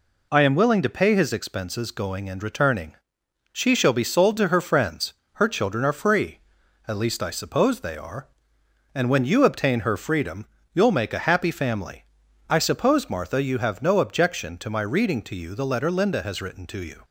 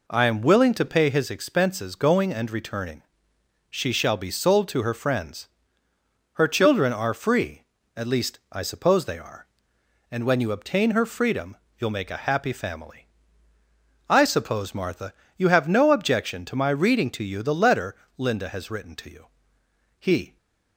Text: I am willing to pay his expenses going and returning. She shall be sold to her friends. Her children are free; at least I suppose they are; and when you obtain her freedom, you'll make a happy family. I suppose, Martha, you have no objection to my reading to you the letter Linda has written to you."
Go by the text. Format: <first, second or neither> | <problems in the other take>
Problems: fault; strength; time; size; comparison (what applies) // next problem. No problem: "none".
first | pauses between "letter" and "Linda"; slight; at 17.9 s; 0.20 s long // goes on to say "He"; slight; from 19.9 s on; 0.38 s long